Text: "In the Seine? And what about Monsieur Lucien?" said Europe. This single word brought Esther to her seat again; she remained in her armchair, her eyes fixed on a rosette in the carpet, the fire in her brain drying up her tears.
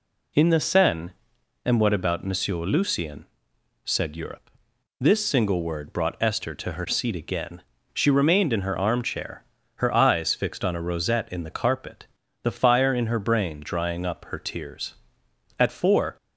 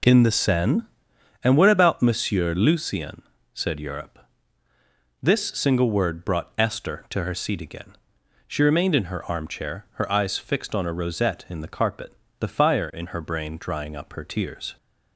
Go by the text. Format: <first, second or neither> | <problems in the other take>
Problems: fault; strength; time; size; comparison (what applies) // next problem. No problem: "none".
second | goes on to say "At four"; from 15.5 s on; 0.60 s long